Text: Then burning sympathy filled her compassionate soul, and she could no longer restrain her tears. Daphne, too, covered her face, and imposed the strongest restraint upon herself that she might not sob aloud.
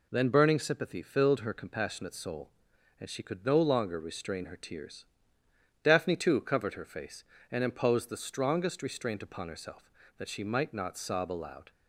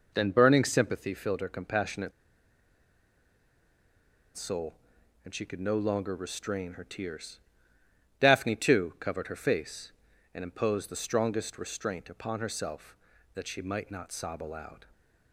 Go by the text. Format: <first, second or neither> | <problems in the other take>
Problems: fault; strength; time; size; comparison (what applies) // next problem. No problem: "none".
first | pauses between "compassionate" and "soul"; strong; at 2.1 s; 2.2 s long